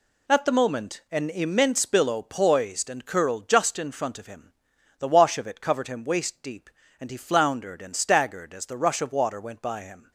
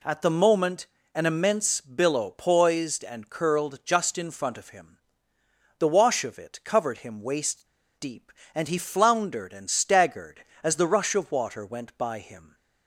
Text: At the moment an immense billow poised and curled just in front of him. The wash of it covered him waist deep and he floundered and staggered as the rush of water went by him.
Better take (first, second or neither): first